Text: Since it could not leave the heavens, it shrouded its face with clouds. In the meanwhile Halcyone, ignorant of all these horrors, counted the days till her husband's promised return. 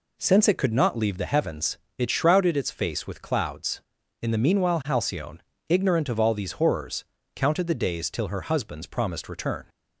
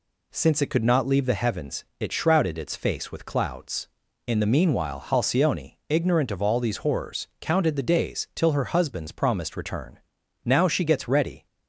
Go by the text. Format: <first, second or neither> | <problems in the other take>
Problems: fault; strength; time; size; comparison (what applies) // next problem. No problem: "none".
first | goes on to say "Now she gets ready"; noticeable; from 10.4 s on; 1.0 s long